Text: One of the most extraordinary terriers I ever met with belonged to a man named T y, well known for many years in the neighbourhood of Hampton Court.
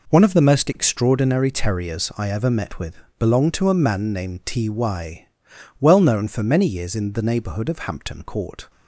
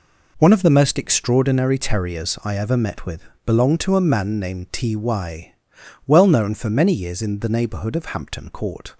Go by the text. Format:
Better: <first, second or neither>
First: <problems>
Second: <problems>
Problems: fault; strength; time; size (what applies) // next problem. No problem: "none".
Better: neither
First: pauses between "with" and "belonged"; slight; at 2.9 s; 0.20 s long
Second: pauses between "with" and "belonged"; slight; at 3.2 s; 0.20 s long